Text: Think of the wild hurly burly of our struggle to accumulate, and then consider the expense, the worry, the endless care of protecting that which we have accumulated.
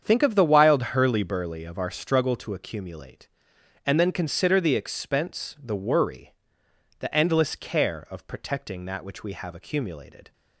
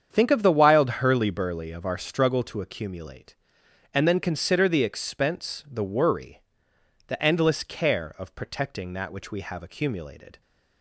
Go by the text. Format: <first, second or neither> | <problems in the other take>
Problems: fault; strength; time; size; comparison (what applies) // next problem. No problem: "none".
neither | starts louder than the rest; strong; the same in both